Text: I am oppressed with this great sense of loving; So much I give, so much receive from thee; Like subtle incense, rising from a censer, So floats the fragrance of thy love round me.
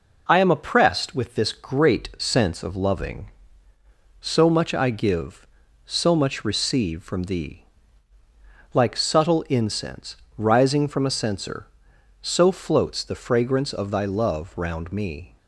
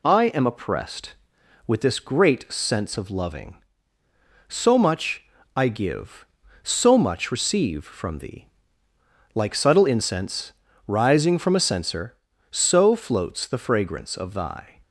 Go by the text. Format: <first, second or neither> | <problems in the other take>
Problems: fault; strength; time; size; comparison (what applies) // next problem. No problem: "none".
first | pauses between "much" and "I"; slight; at 5.2 s; 0.32 s long // stops before "love round me"; at 14.8 s